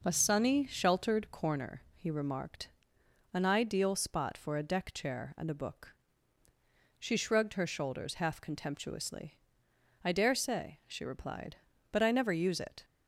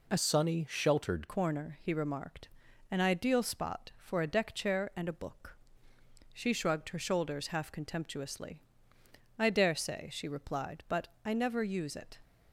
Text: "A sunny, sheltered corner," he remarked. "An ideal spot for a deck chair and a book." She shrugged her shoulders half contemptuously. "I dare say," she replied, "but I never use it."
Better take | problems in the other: first | changes voice from "sunny" to "sheltered"; from 0.1 to 1.2 s; 1.1 s long // pauses between "but" and "I"; slight; at 11.0 s; 0.16 s long

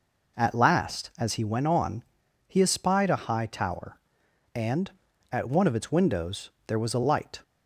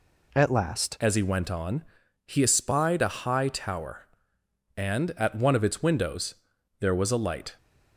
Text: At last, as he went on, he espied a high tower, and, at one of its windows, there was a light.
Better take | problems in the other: first | changes voice at "as"; from 1.0 s on; 6.5 s long

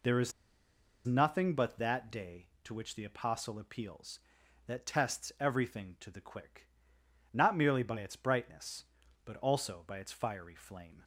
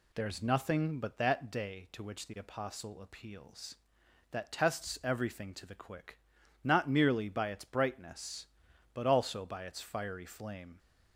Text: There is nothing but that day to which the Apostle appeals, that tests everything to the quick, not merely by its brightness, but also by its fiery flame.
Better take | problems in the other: second | pauses between "is" and "nothing"; noticeable; at 0.3 s; 0.73 s long

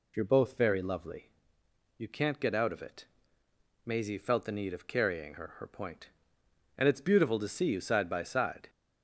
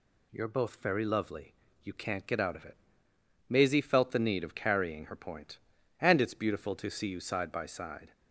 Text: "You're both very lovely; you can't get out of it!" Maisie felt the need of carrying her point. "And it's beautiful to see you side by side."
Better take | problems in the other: second | says "her" twice; at 5.5 s

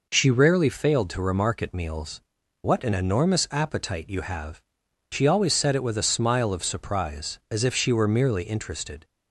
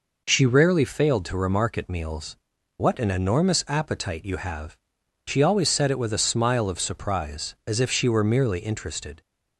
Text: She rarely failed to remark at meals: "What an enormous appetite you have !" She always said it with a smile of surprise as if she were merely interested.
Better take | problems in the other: neither | none

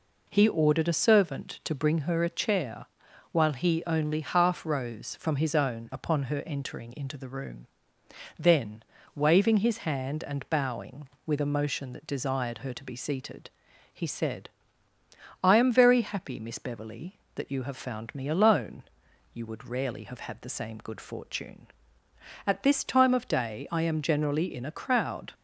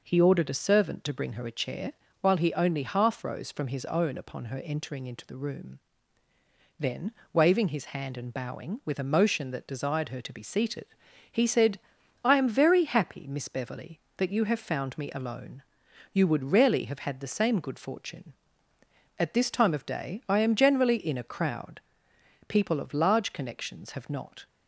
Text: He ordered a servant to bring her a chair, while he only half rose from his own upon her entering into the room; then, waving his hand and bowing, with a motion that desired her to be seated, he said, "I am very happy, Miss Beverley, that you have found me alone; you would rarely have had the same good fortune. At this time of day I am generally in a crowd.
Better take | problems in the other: first | goes on to say "People of large connections have not"; strong; from 22.4 s on; 1.9 s long

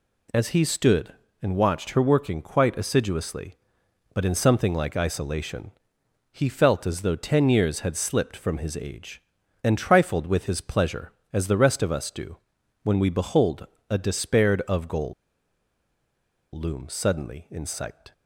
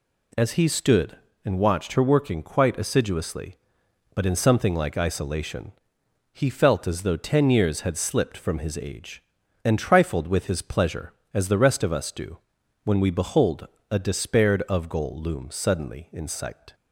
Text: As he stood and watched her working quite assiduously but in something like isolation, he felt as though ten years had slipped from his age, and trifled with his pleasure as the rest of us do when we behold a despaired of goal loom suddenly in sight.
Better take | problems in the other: second | pauses between "do" and "when"; noticeable; at 12.3 s; 0.48 s long; noticeable in the second // pauses between "behold" and "a"; slight; at 13.6 s; 0.22 s long; slight in the second // pauses between "goal" and "loom"; strong; at 15.1 s; 1.4 s long

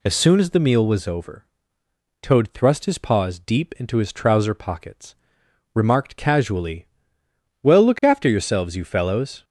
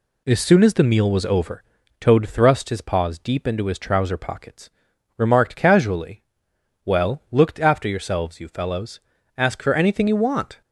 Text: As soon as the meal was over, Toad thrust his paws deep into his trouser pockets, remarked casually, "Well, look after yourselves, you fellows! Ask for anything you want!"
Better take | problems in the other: second | stops before "Ask for anything you want"; at 9.4 s

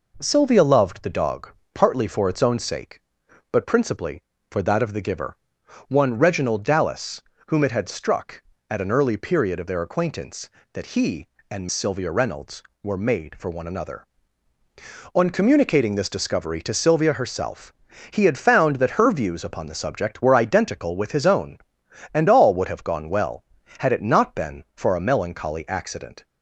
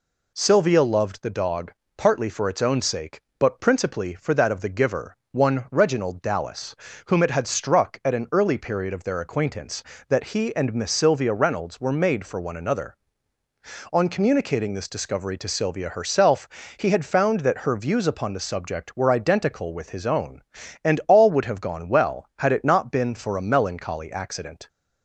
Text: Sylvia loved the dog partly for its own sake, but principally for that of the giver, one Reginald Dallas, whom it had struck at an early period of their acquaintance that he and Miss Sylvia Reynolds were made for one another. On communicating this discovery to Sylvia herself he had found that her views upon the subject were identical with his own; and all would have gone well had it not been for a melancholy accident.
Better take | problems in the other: second | pauses between "dog" and "partly"; slight; at 1.5 s; 0.22 s long; slight in the second // skips "Miss"; at 11.6 s // pauses between "herself" and "he"; at 17.7 s; 0.38 s long; slight in the second

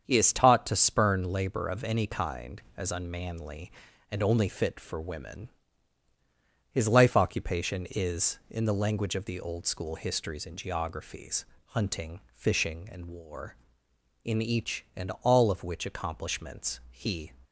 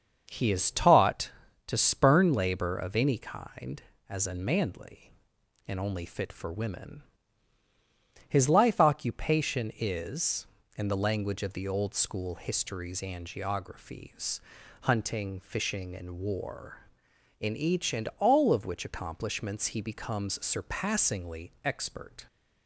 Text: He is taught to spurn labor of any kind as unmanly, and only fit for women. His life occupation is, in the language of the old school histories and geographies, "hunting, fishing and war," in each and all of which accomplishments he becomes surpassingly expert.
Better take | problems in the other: second | starts louder than the rest; strong; until 1.0 s; 7.5 dB; also in the second // stops before "becomes surpassingly expert"; at 17.4 s

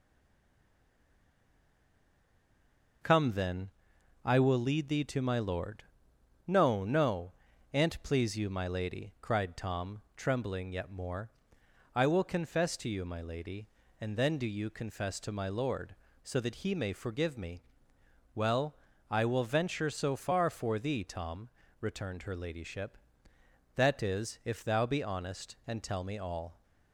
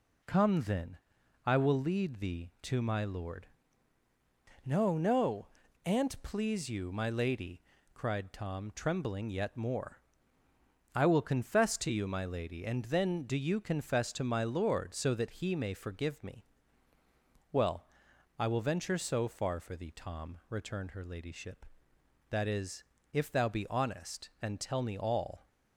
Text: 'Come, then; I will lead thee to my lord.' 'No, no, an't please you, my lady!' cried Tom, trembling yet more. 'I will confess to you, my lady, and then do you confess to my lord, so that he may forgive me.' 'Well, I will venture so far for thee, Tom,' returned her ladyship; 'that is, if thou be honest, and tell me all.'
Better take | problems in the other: second | stays silent before the first word; strong; until 3.0 s; 3.0 s long

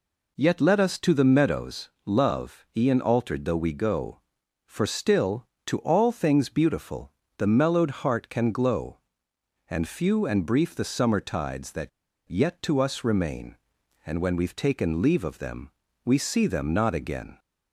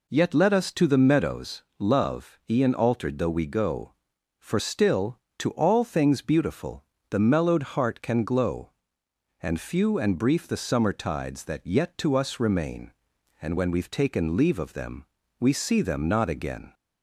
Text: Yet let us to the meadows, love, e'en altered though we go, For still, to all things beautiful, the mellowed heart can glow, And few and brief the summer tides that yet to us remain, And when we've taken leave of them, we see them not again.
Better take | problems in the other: second | pauses between "that" and "yet"; at 11.8 s; 0.38 s long

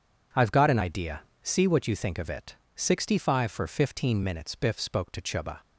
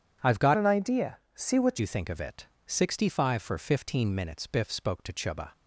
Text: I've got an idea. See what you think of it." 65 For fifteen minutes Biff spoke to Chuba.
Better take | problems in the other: first | changes voice from "an" to "what"; from 0.5 to 1.7 s; 1.2 s long

